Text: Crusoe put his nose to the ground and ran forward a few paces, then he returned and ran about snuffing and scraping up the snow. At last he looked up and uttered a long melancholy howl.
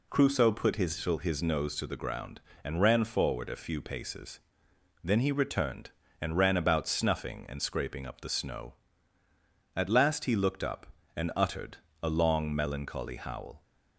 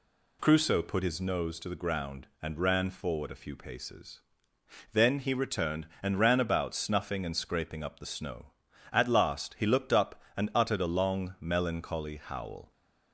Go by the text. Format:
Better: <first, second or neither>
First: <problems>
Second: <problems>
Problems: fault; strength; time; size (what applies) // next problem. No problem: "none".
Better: second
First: says "his" twice; at 1.2 s // pauses between "uttered" and "a"; slight; at 11.7 s; 0.26 s long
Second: none